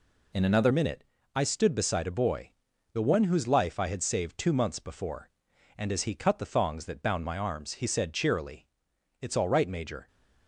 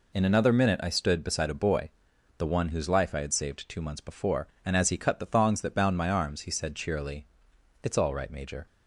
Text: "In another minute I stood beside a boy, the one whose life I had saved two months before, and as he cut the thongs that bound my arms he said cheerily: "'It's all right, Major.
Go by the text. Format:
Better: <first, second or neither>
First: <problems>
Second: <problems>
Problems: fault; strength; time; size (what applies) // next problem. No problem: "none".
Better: second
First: changes voice at "minute"; from 0.7 s on; 9.3 s long // pauses between "minute" and "I"; slight; at 1.0 s; 0.32 s long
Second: none